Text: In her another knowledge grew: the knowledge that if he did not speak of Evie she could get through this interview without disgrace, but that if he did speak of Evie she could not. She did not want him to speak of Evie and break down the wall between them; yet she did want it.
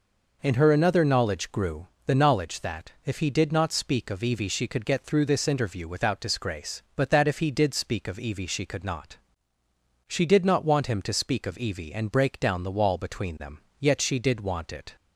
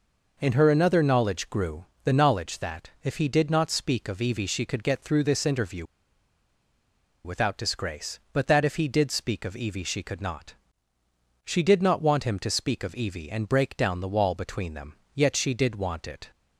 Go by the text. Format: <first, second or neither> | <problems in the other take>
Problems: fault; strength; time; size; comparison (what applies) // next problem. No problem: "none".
first | pauses between "interview" and "without"; strong; at 5.8 s; 1.4 s long